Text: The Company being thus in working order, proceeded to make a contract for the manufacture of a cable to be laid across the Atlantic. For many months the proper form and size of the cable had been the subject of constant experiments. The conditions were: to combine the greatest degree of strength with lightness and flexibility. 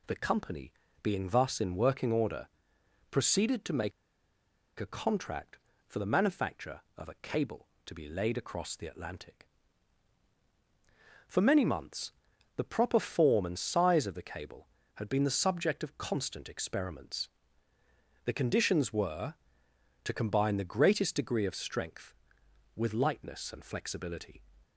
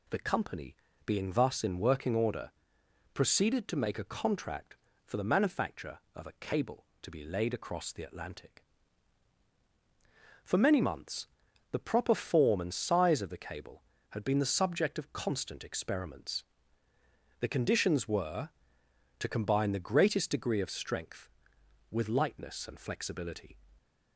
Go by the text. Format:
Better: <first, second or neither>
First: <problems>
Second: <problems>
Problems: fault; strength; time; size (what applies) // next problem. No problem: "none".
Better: second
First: pauses between "Company" and "being"; slight; at 0.7 s; 0.28 s long // pauses between "make" and "a"; noticeable; at 3.9 s; 0.88 s long // pauses between "months" and "the"; at 12.1 s; 0.44 s long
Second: pauses between "Company" and "being"; slight; at 0.7 s; 0.28 s long // pauses between "months" and "the"; at 11.2 s; 0.44 s long